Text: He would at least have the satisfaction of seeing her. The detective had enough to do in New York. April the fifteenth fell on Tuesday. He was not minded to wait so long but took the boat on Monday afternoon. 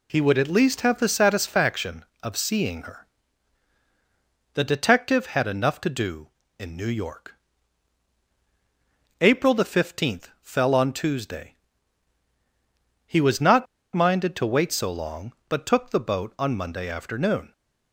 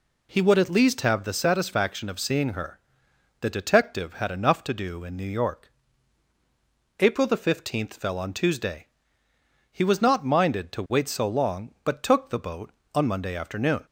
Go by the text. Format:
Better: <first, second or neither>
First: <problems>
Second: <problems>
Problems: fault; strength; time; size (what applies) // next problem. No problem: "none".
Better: second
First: pauses between "not" and "minded"; slight; at 13.6 s; 0.30 s long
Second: none